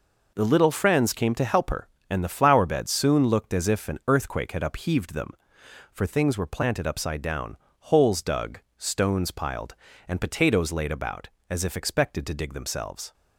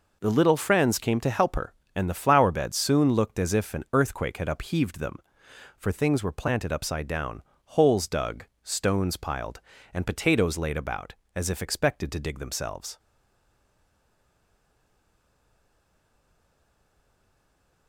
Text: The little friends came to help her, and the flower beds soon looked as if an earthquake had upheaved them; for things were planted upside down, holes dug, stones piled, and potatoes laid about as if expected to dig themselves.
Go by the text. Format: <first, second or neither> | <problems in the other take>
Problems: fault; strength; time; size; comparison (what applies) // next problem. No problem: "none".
first | stays silent after the last word; strong; from 12.9 s on; 4.9 s long